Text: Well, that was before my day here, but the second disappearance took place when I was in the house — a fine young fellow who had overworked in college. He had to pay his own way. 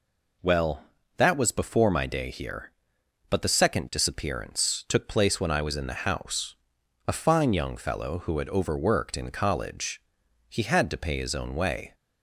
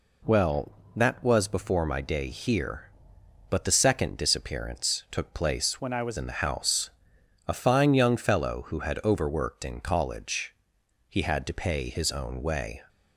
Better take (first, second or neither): first